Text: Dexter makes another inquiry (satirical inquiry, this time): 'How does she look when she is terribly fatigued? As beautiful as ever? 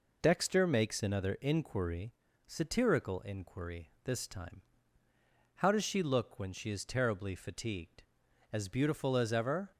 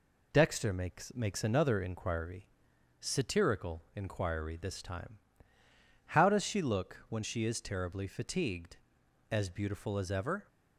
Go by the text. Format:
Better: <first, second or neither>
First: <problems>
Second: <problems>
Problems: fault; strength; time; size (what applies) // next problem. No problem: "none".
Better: first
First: none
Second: says "makes" twice; at 1.1 s